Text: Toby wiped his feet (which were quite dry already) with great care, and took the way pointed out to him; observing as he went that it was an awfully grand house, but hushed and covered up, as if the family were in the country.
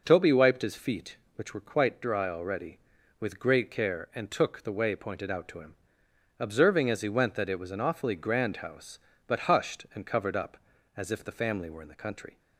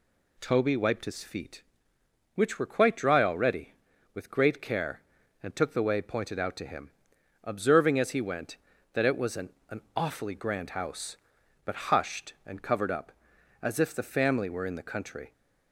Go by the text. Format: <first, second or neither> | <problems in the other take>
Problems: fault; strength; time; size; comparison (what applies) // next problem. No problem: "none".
first | says "an" twice; at 9.7 s